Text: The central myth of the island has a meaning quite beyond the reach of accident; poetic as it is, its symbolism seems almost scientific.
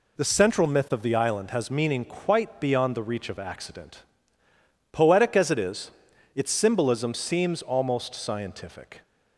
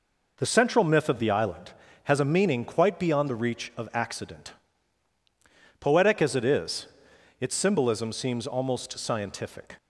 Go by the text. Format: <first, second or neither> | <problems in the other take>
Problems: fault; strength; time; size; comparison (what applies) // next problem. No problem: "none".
second | skips "a"; at 1.6 s